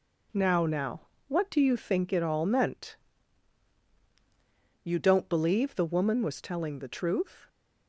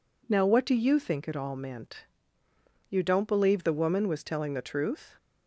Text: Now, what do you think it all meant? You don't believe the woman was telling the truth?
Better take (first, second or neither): second